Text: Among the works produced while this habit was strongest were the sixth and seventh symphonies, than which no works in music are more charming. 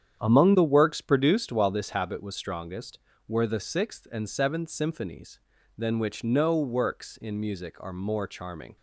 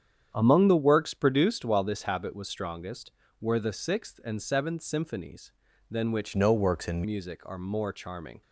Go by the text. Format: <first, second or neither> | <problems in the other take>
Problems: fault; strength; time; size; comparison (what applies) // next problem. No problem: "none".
first | starts louder than the rest; strong; until 1.3 s; 8.5 dB; strong in the first // changes voice from "no" to "in"; from 6.3 to 7.0 s; 0.7 s long